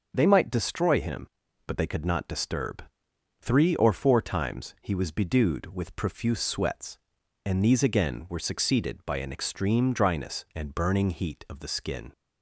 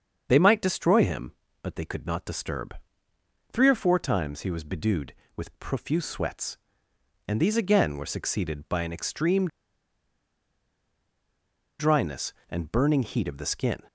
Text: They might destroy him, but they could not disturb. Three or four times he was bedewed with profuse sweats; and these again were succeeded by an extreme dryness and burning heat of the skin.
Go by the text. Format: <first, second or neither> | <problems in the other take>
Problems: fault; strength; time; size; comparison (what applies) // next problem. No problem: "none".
first | starts louder than the rest; strong; until 1.2 s; 7 dB; also in the first // pauses between "extreme" and "dryness"; strong; at 9.4 s; 2.3 s long